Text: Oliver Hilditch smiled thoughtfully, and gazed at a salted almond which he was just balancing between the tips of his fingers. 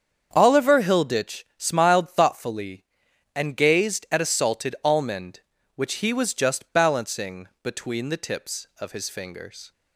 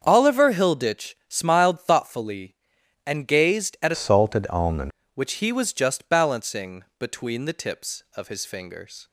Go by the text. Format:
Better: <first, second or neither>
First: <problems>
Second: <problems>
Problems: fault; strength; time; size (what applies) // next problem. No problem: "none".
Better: first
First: starts louder than the rest; strong; until 1.3 s; 7.5 dB // pauses between "balancing" and "between"; slight; at 7.4 s; 0.16 s long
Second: starts louder than the rest; until 1.0 s; 7 dB // changes voice from "salted" to "almond"; from 3.9 to 4.9 s; 1.0 s long // pauses between "balancing" and "between"; slight; at 6.8 s; 0.16 s long